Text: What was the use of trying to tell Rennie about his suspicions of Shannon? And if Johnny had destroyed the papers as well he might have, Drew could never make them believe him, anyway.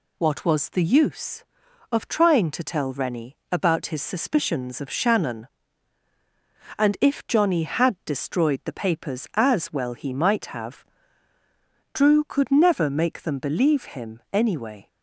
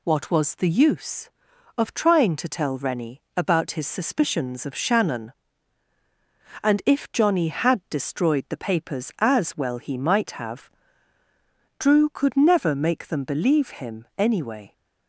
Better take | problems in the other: neither | pauses between "Rennie" and "about"; slight; the same in both

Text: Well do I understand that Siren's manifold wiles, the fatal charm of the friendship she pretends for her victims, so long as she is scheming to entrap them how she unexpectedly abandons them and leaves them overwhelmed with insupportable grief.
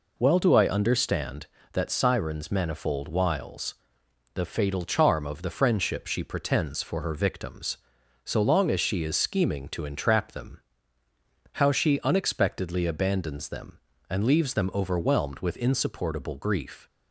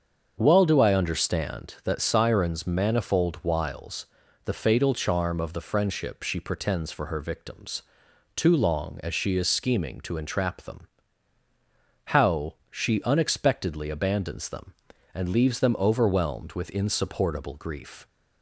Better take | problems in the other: first | starts louder than the rest; until 1.3 s; 7 dB // says "too" for "so"; at 8.3 s // pauses between "them" and "how"; strong; at 10.8 s; 1.2 s long; noticeable in the first // pauses between "how" and "she"; slight; at 12.5 s; 0.16 s long

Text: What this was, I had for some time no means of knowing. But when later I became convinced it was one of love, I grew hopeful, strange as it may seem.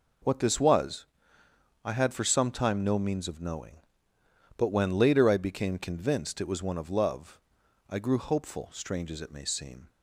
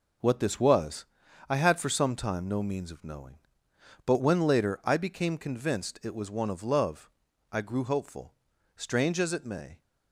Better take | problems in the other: first | stops before "seem"; at 9.8 s

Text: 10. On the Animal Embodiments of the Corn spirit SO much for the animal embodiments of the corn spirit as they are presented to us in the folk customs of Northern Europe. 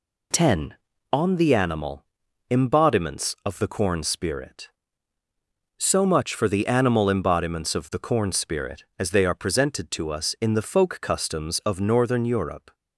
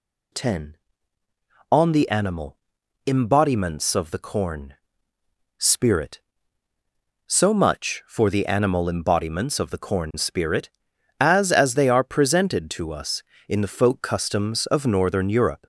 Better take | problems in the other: first | pauses between "Animal" and "Embodiments"; noticeable; at 2.5 s; 0.48 s long; also in the first // pauses between "Corn" and "spirit"; noticeable; at 4.7 s; 0.84 s long // says "as" twice; at 11.4 s

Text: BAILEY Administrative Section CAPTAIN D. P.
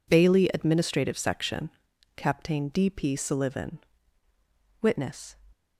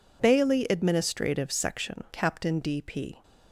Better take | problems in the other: second | pauses between "Section" and "CAPTAIN"; noticeable; at 1.6 s; 0.48 s long // goes on to say "SULLIVAN Witness"; strong; from 3.1 s on; 2.2 s long

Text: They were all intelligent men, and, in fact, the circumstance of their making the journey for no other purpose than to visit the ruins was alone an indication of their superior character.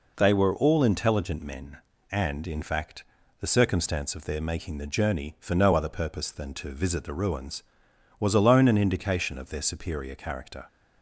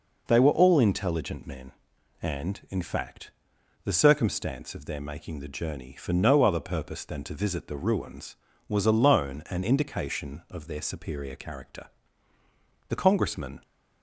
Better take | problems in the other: first | goes on to say "The Congressman"; noticeable; from 12.8 s on; 0.76 s long

